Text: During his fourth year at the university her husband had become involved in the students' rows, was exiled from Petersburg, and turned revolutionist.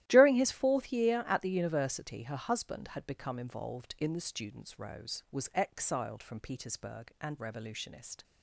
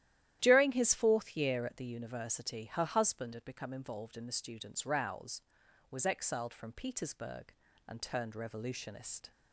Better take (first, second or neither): second